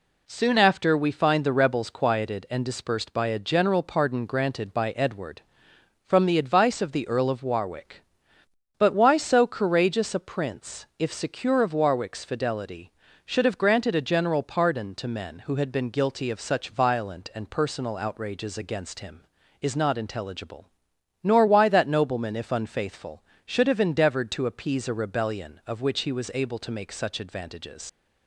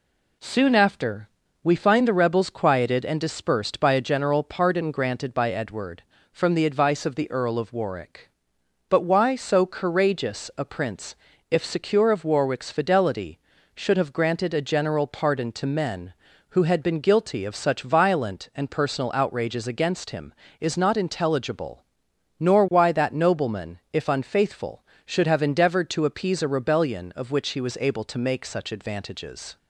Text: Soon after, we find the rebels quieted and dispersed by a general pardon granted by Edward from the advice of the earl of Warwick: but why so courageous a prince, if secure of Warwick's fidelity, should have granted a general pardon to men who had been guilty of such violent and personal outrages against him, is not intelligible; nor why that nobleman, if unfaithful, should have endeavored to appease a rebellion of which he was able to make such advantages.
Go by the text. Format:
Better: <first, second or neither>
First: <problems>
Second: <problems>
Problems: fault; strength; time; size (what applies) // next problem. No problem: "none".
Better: second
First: leaves "advantages" unfinished; at 27.8 s; 85 ms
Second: none